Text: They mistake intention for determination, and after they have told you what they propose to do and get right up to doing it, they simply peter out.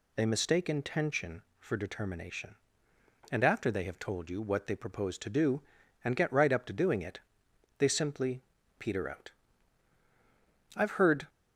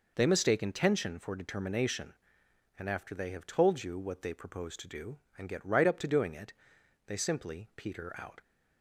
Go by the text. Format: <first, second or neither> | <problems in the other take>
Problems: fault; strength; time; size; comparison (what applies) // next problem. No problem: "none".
second | pauses between "simply" and "peter"; slight; at 8.4 s; 0.34 s long // goes on to say "I've heard"; from 10.7 s on; 0.52 s long